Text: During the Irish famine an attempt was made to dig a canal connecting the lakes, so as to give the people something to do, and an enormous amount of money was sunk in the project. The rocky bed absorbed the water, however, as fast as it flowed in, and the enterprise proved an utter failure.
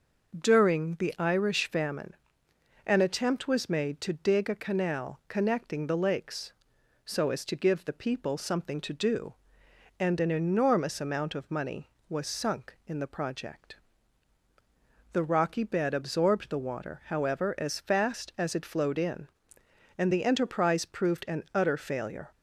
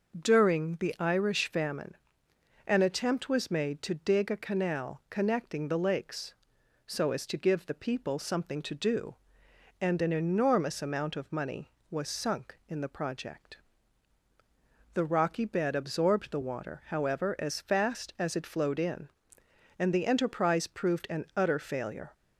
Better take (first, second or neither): neither